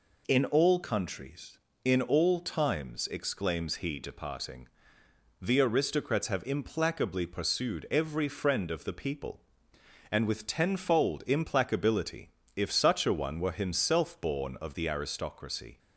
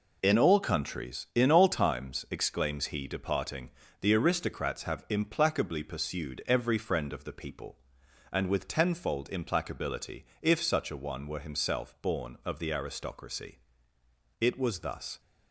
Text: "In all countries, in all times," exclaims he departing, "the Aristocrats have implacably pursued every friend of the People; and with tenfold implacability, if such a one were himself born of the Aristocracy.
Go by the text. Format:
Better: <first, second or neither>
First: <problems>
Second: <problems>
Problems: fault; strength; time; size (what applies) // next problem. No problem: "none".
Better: first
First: none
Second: goes on to say "It was thus"; noticeable; from 14.4 s on; 0.80 s long